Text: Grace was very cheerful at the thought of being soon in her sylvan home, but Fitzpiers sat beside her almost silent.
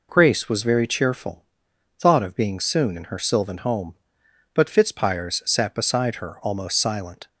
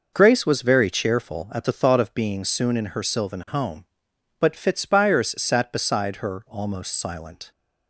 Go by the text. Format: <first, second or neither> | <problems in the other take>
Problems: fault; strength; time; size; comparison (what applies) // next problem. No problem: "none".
second | skips "at the"; at 1.7 s